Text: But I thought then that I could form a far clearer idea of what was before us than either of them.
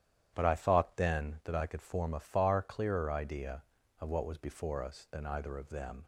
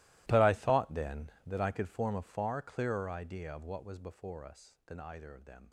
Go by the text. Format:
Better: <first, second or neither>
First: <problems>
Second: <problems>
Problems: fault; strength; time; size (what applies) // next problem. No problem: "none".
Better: first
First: starts louder than the rest; strong; until 1.3 s; 11 dB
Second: gets quieter; strong; throughout; 19.5 dB // starts louder than the rest; strong; until 1.2 s; 18.5 dB